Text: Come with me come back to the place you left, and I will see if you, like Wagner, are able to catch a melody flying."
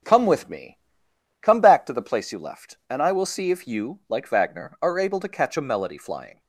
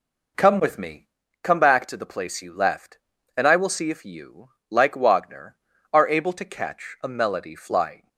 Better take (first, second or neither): second